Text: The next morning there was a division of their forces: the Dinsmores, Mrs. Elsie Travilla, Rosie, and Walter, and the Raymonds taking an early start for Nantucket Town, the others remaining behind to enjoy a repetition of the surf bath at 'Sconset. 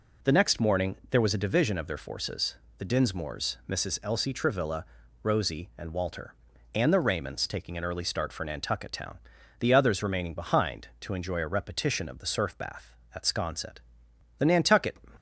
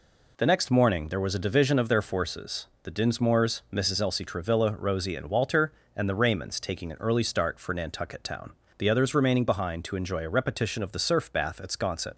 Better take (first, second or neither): second